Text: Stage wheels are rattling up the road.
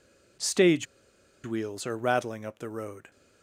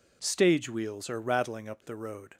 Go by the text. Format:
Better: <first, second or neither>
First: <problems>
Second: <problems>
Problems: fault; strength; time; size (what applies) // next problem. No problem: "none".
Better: second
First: pauses between "Stage" and "wheels"; noticeable; at 0.8 s; 0.58 s long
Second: none